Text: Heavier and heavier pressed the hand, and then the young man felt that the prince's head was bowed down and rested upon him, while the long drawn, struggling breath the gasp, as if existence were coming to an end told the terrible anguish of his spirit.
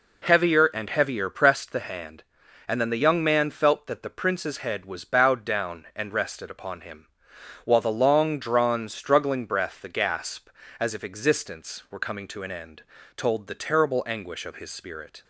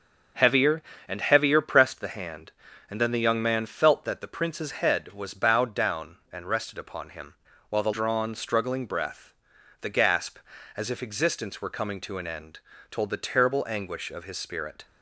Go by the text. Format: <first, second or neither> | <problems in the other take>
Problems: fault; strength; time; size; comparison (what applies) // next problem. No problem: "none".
first | starts louder than the rest; until 1.6 s; 7 dB // skips "long"; at 7.9 s // pauses between "breath" and "the"; noticeable; at 9.3 s; 0.48 s long // pauses between "end" and "told"; slight; at 12.5 s; 0.30 s long; slight in the first